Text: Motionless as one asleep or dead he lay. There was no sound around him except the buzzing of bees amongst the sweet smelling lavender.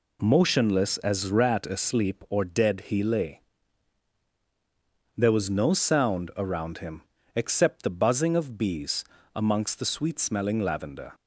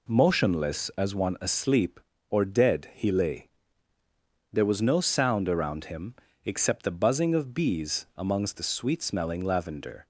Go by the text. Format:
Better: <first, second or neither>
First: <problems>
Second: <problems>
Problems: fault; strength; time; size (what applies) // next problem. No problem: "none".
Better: second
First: says "rat" for "one"; at 1.3 s // pauses between "him" and "except"; slight; at 7.0 s; 0.34 s long // pauses between "bees" and "amongst"; slight; at 9.0 s; 0.32 s long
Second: pauses between "him" and "except"; slight; at 6.1 s; 0.30 s long